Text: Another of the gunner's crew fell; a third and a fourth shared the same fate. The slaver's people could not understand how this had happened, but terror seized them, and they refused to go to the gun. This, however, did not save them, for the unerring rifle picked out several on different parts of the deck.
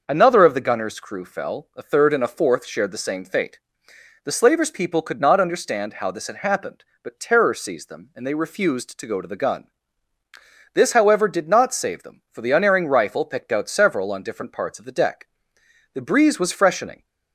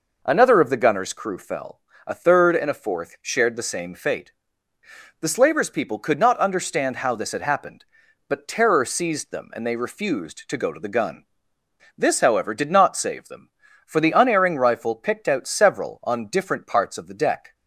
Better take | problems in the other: second | starts louder than the rest; noticeable; until 1.0 s; 6 dB // goes on to say "The breeze was freshening"; noticeable; from 15.9 s on; 1.1 s long

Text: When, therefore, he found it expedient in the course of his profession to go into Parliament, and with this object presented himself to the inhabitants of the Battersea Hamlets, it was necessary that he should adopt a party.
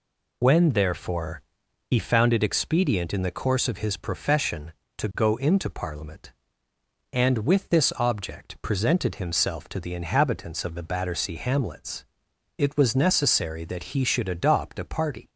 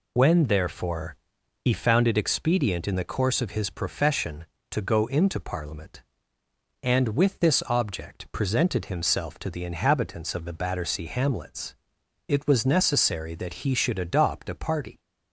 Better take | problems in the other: neither | none

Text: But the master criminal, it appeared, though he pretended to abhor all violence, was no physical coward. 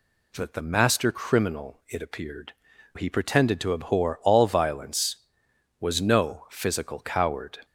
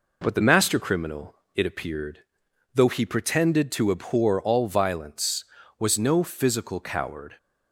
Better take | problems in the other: second | skips "though"; at 2.7 s

